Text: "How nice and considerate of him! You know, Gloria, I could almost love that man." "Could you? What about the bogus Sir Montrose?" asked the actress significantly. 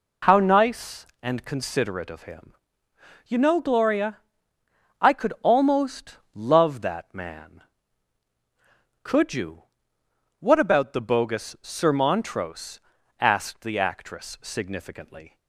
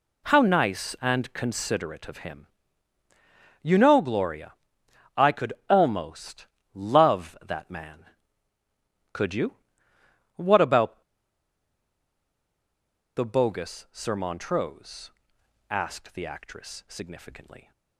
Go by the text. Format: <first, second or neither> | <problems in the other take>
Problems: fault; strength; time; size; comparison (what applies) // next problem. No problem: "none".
first | pauses between "could" and "almost"; slight; at 5.5 s; 0.16 s long // pauses between "almost" and "love"; slight; at 6.4 s; 0.26 s long; slight in the first // pauses between "about" and "the"; strong; at 11.0 s; 2.1 s long